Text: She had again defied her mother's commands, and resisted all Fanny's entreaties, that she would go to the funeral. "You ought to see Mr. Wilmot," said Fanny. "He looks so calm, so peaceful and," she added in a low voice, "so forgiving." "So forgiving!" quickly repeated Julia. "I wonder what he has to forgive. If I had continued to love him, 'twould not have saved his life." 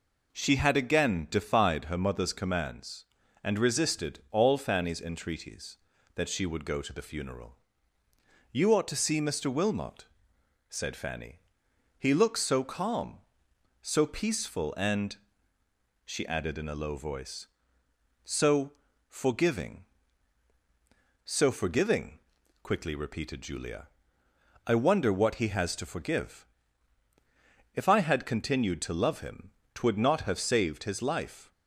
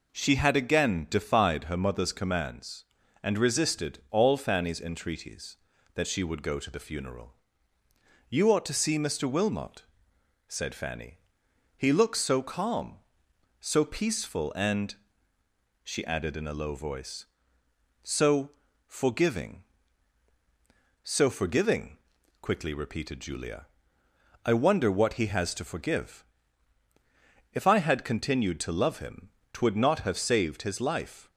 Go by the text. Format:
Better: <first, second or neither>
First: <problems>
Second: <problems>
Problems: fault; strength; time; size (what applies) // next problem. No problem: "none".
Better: neither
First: pauses between "so" and "forgiving"; slight; at 18.7 s; 0.34 s long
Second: pauses between "so" and "forgiving"; slight; at 18.5 s; 0.34 s long